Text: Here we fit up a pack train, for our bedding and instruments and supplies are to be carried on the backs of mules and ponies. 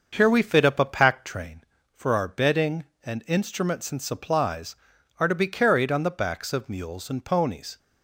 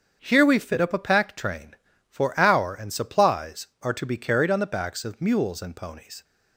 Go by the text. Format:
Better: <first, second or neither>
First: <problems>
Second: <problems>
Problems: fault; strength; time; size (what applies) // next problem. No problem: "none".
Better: first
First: starts louder than the rest; until 1.1 s; 6.5 dB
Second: starts louder than the rest; strong; until 1.2 s; 7.5 dB // skips "bedding and instruments"; at 2.7 s